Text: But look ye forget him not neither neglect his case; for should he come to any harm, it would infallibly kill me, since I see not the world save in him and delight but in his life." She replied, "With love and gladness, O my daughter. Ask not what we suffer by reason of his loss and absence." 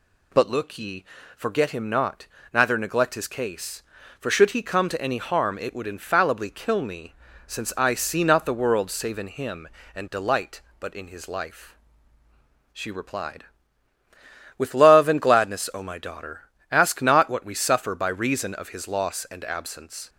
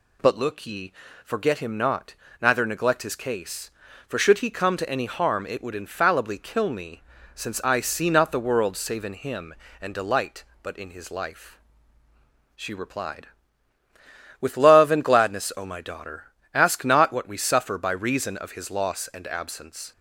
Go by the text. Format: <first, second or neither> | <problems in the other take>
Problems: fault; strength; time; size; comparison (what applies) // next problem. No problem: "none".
neither | pauses between "ye" and "forget"; slight; the same in both // pauses between "not" and "neither"; slight; the same in both